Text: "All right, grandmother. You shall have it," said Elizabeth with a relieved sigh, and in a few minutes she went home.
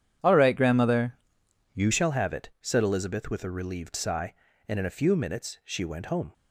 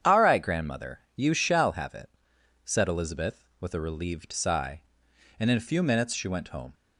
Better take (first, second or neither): second